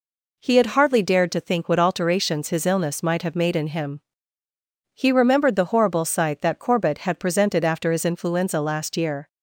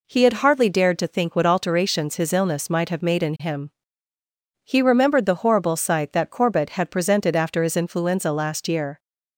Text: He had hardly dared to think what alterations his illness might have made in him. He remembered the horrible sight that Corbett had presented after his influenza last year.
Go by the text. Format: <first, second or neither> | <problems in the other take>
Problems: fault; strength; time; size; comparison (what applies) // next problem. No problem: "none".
neither | none